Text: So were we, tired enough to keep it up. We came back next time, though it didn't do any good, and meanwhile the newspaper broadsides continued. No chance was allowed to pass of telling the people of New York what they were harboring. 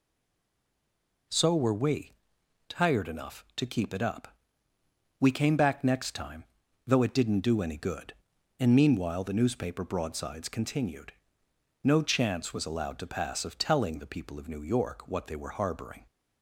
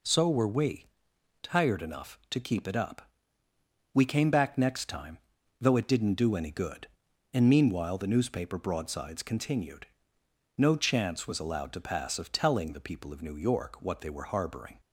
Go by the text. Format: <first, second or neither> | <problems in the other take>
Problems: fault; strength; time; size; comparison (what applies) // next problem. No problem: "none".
second | stays silent before the first word; noticeable; until 1.2 s; 1.2 s long